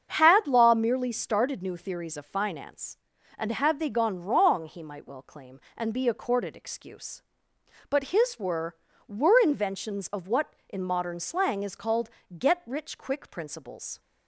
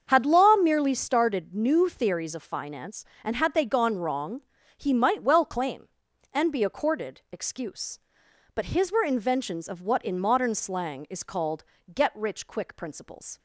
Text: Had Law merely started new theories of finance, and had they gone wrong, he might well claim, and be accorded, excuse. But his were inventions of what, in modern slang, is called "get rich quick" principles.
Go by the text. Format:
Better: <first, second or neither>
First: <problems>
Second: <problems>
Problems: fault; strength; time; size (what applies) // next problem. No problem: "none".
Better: second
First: starts louder than the rest; strong; until 1.1 s; 7 dB // says "were" twice; at 9.0 s // pauses between "called" and "get"; slight; at 12.0 s; 0.26 s long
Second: starts louder than the rest; until 1.0 s; 7 dB // pauses between "called" and "get"; slight; at 11.6 s; 0.32 s long